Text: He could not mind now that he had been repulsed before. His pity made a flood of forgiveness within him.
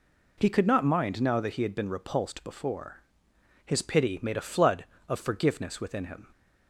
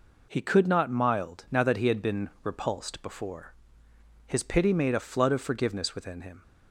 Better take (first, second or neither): first